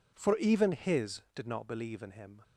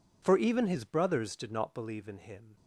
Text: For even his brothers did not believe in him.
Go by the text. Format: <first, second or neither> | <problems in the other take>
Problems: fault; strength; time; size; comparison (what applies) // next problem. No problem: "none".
second | skips "brothers"; at 1.2 s